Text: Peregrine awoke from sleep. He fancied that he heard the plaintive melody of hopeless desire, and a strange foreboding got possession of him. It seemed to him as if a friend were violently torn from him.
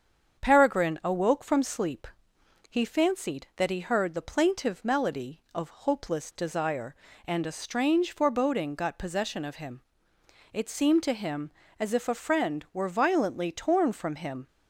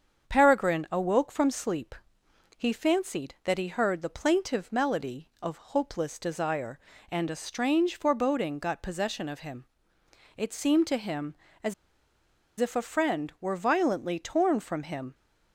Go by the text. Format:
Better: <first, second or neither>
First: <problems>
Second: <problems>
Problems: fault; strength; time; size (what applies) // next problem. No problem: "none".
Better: first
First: starts louder than the rest; strong; until 1.4 s; 7.5 dB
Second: starts louder than the rest; strong; until 1.3 s; 7.5 dB // pauses between "as" and "if"; noticeable; at 11.7 s; 0.86 s long